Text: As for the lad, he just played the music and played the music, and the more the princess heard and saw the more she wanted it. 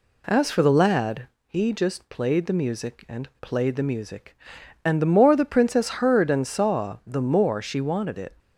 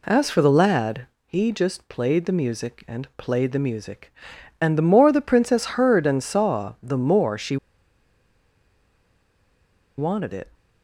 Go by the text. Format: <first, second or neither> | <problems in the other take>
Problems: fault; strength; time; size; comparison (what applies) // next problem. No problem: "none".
first | pauses between "she" and "wanted"; strong; at 7.5 s; 2.4 s long